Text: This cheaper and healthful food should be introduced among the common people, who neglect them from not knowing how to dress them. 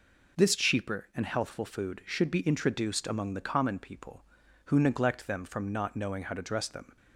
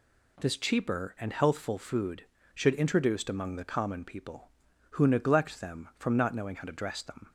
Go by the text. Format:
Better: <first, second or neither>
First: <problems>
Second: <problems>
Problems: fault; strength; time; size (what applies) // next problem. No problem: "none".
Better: first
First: none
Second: skips "be"; at 2.7 s